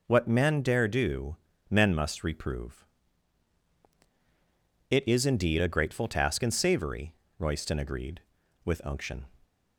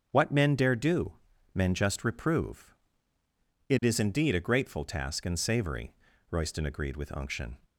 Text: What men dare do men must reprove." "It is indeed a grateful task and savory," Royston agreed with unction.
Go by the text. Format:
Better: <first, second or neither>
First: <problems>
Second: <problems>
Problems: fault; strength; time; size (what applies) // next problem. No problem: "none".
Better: first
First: pauses between "do" and "men"; slight; at 1.3 s; 0.34 s long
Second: starts louder than the rest; until 1.1 s; 7 dB // pauses between "do" and "men"; at 1.1 s; 0.40 s long // says "just" for "must"; at 1.7 s